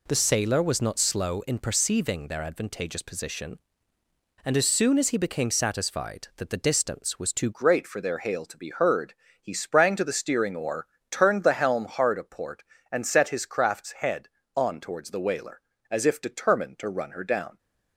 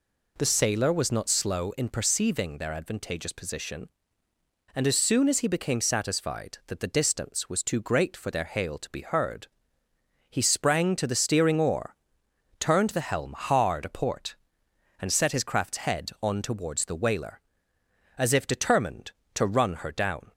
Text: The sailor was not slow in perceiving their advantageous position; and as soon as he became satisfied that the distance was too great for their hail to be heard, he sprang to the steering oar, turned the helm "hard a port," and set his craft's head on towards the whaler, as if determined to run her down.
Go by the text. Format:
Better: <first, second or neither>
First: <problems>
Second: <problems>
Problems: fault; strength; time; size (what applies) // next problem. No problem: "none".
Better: second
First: changes voice at "great"; from 7.5 s on; 10.0 s long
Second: none